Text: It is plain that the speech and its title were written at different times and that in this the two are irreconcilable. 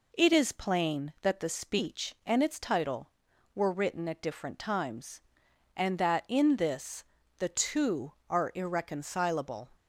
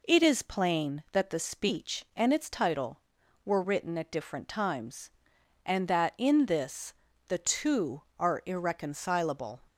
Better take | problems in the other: neither | pauses between "this" and "the"; slight; the same in both

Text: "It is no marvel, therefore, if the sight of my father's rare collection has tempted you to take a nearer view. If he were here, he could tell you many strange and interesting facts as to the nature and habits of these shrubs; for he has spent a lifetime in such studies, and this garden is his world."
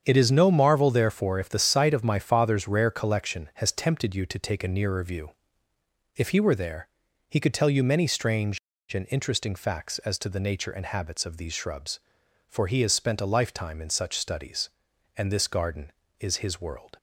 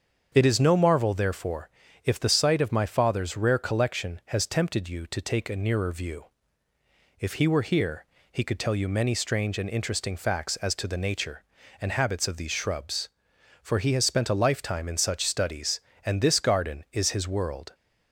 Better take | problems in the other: second | starts louder than the rest; strong; until 1.0 s; 7.5 dB; strong in the second // says "there" for "here"; at 6.5 s

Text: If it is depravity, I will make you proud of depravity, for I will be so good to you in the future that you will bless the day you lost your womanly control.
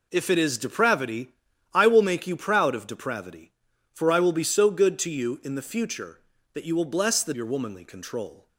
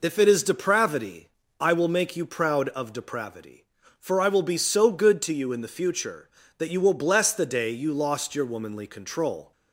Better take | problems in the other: second | skips "day you lost"; at 7.3 s

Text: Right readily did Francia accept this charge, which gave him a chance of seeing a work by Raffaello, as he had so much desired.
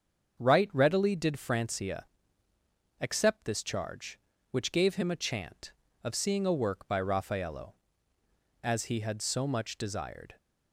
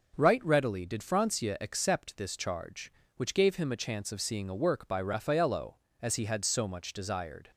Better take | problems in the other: second | starts louder than the rest; until 1.4 s; 7 dB; also in the second // pauses between "Francia" and "accept"; noticeable; at 2.0 s; 0.96 s long // says "chant" for "chance"; at 5.1 s

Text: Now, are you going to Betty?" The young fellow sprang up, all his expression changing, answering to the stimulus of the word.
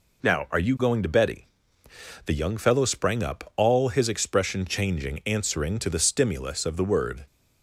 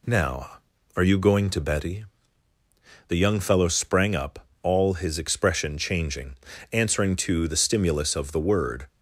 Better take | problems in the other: neither | none

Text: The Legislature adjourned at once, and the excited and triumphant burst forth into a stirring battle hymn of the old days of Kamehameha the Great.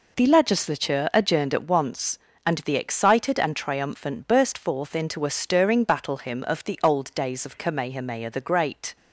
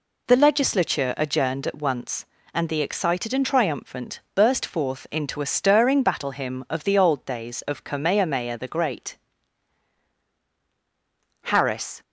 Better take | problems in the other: first | goes on to say "Harris"; from 11.4 s on; 0.60 s long

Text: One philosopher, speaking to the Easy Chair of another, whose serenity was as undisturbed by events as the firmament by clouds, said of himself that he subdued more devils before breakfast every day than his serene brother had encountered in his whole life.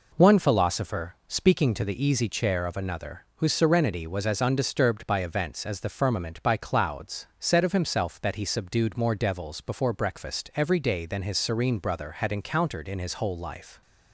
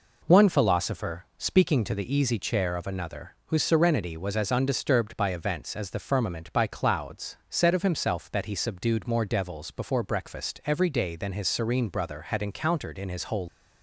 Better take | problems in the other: first | stops before "life"; at 13.4 s

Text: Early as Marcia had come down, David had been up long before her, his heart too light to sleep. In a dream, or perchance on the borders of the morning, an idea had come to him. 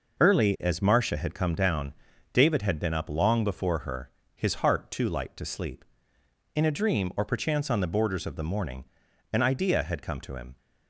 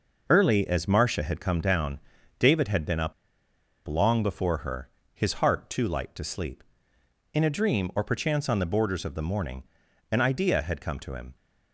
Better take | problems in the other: first | pauses between "up" and "long"; noticeable; at 3.1 s; 0.74 s long

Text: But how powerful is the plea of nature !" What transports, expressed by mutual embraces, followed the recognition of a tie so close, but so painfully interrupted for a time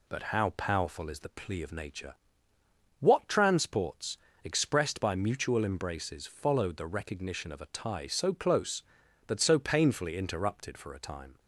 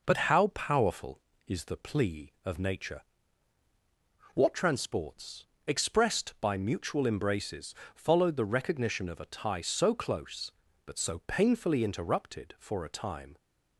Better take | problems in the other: neither | none

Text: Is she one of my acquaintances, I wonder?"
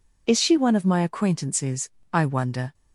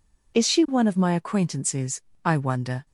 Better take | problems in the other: neither | none

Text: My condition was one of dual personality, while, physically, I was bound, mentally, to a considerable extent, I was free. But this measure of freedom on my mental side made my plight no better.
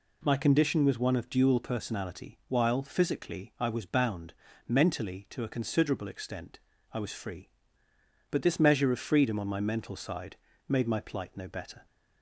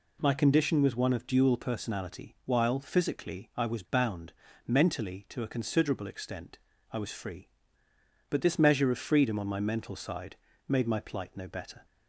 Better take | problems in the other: neither | pauses between "side" and "made"; slight; the same in both

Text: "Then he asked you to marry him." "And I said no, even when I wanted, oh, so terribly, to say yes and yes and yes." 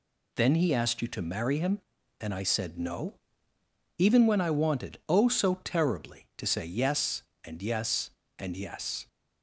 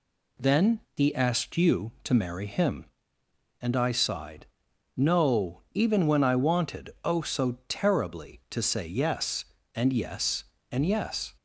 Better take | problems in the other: first | says "sighed" for "said"; at 3.9 s

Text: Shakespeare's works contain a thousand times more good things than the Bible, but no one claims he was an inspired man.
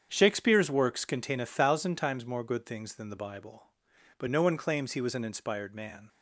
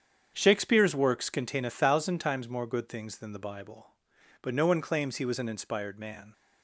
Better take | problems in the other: neither | starts louder than the rest; strong; the same in both

